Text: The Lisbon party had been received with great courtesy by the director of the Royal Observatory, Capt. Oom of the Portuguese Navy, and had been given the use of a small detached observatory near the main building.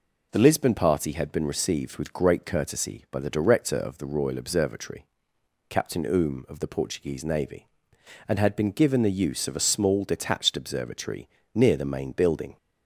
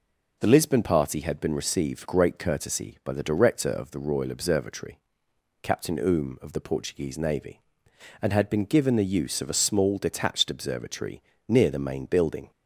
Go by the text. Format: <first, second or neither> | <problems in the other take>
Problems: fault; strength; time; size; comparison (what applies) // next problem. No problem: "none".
first | skips "with"; at 2.0 s // pauses between "observatory" and "near"; slight; at 11.2 s; 0.26 s long; slight in the first